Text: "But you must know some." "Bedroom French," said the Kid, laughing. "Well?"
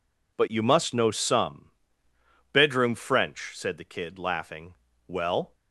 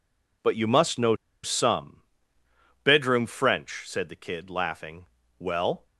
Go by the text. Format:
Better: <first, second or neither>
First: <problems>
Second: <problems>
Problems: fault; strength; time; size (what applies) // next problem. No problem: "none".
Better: first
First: none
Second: pauses between "know" and "some"; slight; at 1.1 s; 0.27 s long